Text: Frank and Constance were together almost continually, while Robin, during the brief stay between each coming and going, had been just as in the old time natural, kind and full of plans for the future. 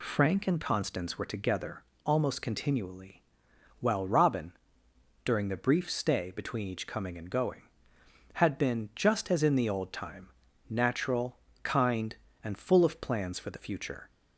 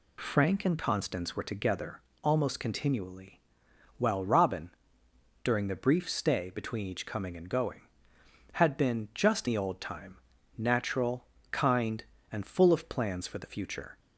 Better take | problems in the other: first | pauses between "together" and "almost"; slight; at 2.0 s; 0.22 s long; slight in the first // skips "as in"; at 9.4 s // pauses between "time" and "natural"; at 10.1 s; 0.40 s long; also in the first

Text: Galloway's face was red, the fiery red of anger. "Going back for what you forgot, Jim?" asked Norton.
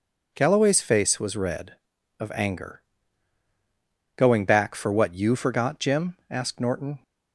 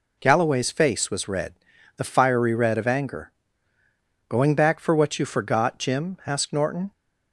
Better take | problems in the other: second | skips "the fiery red"; at 1.9 s

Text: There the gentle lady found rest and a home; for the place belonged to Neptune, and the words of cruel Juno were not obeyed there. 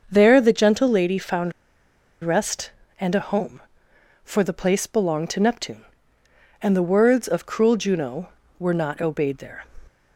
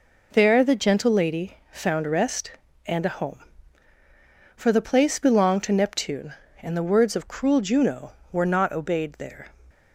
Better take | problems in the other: second | starts louder than the rest; until 1.1 s; 6.5 dB // pauses between "found" and "rest"; noticeable; at 1.5 s; 0.71 s long

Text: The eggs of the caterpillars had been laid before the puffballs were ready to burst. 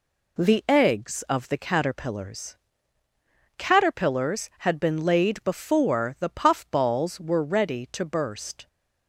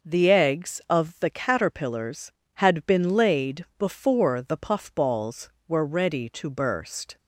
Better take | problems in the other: second | says "caterpillars" twice; at 3.5 s

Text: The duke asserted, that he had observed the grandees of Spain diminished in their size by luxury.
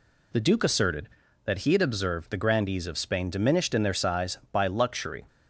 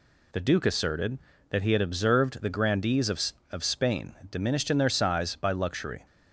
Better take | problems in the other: first | says "of" twice; at 3.5 s

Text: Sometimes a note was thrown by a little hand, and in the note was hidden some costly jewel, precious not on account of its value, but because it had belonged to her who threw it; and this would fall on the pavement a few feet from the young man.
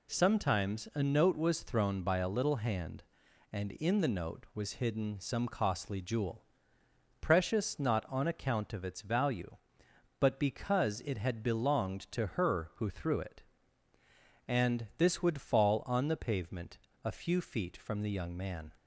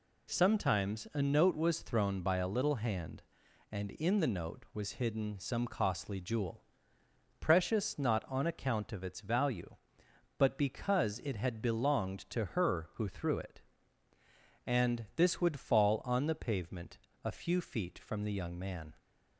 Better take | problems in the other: neither | pauses between "pavement" and "a"; slight; the same in both

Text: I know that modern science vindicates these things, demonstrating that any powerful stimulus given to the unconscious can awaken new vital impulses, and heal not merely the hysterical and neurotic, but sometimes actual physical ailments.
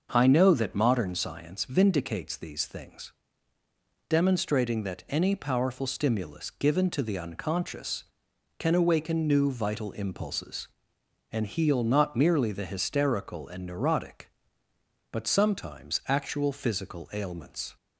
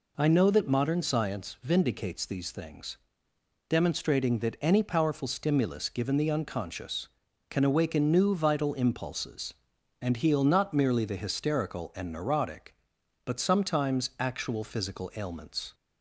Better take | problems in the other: first | skips "to"; at 6.1 s

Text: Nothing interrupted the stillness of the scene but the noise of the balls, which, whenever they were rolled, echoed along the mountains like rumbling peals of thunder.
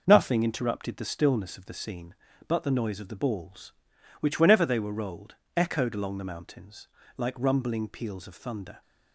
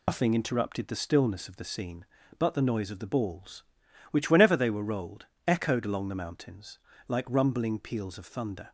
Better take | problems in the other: first | loses the start of "Nothing"; at 0.0 s; 100 ms // pauses between "mountains" and "like"; slight; at 6.7 s; 0.30 s long; slight in the first

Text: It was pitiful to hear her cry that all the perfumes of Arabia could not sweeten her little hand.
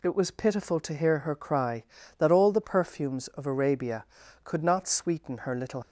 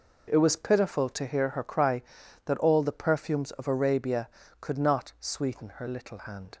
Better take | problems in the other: second | stops before "hand"; at 5.8 s

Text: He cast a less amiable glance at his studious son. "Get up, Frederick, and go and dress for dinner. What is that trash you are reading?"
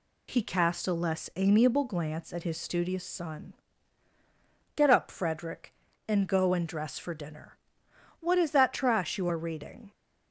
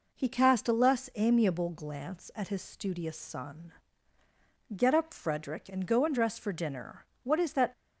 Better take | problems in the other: first | stops before "trash you are reading"; at 7.7 s

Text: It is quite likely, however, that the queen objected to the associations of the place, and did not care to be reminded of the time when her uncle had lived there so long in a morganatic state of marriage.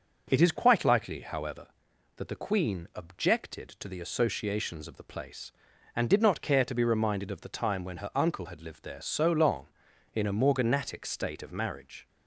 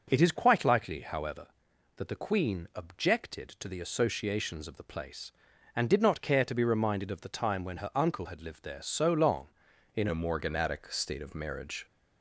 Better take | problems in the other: first | changes voice at "a"; from 10.0 s on; 1.8 s long

